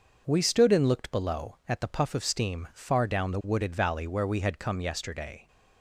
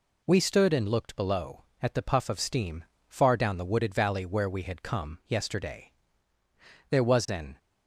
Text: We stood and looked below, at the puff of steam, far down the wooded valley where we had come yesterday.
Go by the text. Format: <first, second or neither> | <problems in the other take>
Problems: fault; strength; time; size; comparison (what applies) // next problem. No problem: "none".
first | goes on to say "There was an"; noticeable; from 6.9 s on; 0.66 s long